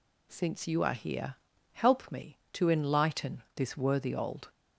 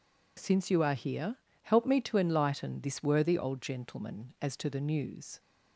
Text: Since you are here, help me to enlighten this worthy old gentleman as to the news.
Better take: second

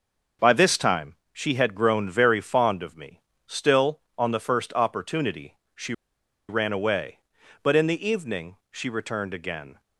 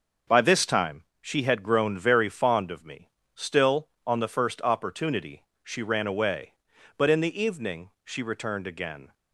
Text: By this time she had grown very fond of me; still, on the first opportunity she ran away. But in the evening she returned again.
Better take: second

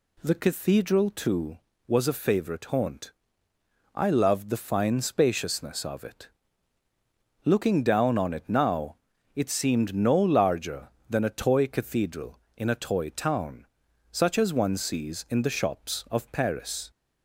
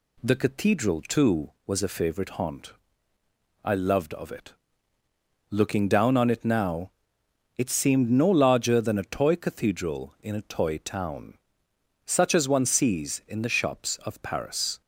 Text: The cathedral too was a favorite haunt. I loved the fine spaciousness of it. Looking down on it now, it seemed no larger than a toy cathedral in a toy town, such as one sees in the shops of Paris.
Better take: first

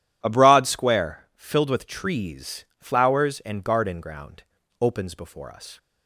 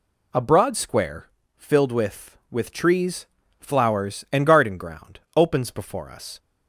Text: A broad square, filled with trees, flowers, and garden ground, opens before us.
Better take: first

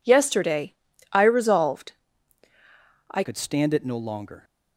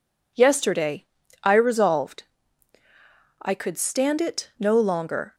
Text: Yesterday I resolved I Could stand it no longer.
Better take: second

